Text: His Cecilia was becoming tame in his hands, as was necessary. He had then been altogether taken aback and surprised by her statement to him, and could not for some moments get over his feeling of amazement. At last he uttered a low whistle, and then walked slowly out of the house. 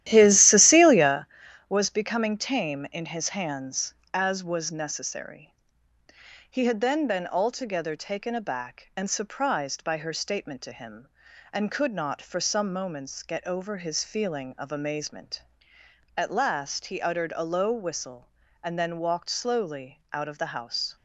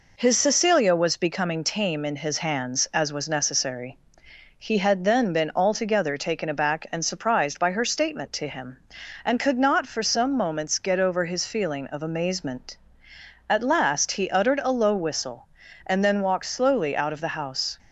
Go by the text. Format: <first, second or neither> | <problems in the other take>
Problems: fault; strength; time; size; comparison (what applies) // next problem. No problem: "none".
second | starts louder than the rest; strong; until 1.2 s; 13 dB